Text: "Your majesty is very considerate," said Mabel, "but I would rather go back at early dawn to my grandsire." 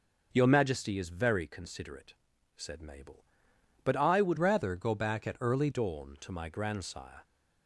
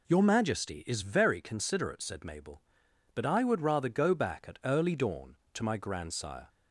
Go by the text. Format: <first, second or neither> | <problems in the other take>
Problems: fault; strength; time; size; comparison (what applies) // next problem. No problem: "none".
second | changes voice from "rather" to "early"; from 4.3 to 5.6 s; 1.3 s long